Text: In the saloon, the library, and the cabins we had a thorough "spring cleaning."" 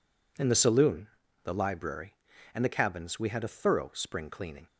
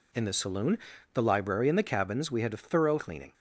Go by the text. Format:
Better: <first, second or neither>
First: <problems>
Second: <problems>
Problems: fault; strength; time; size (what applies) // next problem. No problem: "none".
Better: first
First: none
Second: skips "spring"; at 2.9 s